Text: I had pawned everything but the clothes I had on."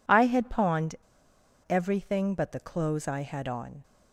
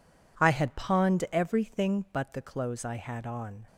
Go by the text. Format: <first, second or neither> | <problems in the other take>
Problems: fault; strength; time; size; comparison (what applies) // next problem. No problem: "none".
second | pauses between "pawned" and "everything"; noticeable; at 0.9 s; 0.71 s long